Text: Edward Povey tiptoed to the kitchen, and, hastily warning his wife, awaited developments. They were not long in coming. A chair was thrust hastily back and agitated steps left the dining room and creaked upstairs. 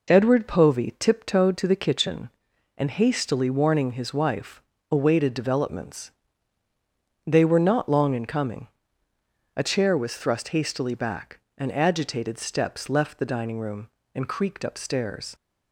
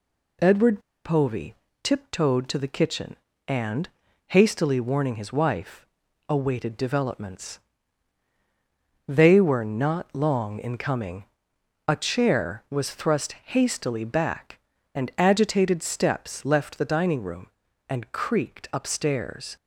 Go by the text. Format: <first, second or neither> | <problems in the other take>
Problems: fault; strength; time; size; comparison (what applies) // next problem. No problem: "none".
first | pauses between "Edward" and "Povey"; slight; at 0.7 s; 0.25 s long // pauses between "Povey" and "tiptoed"; slight; at 1.5 s; 0.26 s long